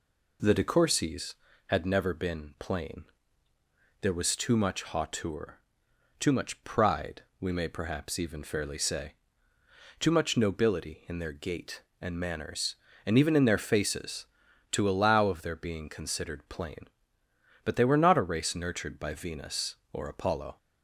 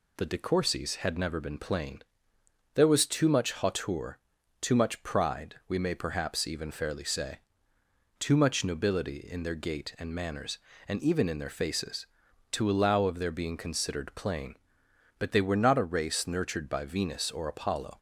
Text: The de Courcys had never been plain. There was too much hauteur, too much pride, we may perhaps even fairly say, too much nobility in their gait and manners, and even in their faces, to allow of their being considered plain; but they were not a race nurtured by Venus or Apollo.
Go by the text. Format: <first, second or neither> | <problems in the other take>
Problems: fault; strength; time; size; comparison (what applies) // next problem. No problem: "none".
neither | none